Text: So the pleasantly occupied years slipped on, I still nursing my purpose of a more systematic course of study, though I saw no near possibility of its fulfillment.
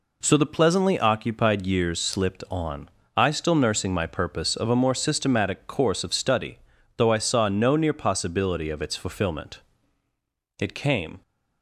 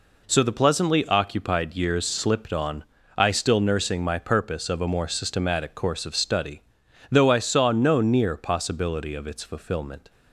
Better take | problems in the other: second | goes on to say "It came"; noticeable; from 10.5 s on; 0.62 s long

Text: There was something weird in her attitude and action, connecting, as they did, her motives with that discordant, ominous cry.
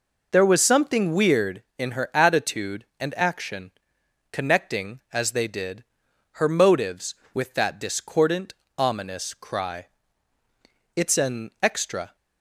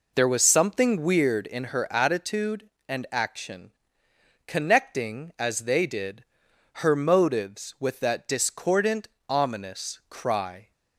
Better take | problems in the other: second | goes on to say "It's an extra"; noticeable; from 10.9 s on; 1.2 s long

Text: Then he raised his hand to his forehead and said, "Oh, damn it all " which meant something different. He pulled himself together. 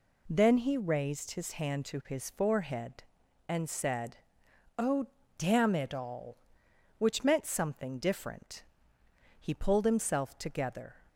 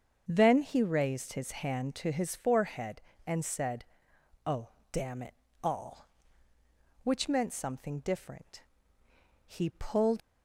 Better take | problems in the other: first | starts louder than the rest; strong; until 1.2 s; 7.5 dB // pauses between "it" and "all"; slight; at 5.3 s; 0.28 s long // stops before "himself together"; at 10.2 s

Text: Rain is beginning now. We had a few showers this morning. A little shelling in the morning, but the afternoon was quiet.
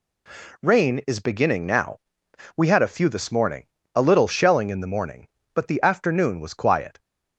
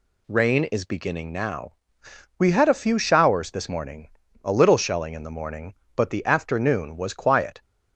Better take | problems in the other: second | skips "showers"; at 3.0 s

